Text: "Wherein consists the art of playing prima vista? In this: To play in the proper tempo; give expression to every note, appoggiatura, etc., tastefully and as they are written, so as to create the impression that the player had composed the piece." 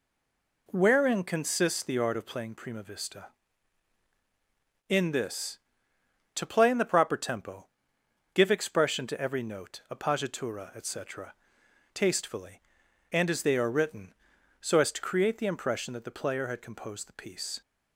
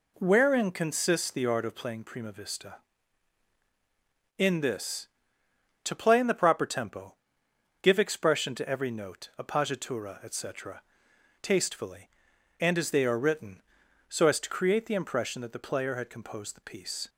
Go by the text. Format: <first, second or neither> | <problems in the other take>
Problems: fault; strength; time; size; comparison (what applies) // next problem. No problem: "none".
second | stays silent before the first word; slight; until 0.6 s; 0.6 s long